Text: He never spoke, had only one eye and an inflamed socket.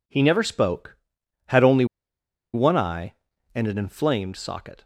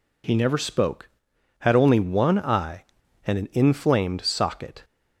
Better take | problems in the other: second | pauses between "only" and "one"; noticeable; at 1.8 s; 0.67 s long

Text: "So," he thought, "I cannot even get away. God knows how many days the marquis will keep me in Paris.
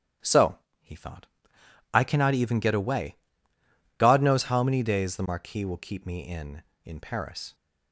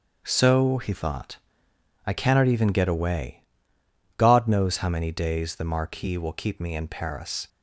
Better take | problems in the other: second | starts louder than the rest; strong; until 2.1 s; 12 dB; also in the second // says "in" twice; at 6.8 s

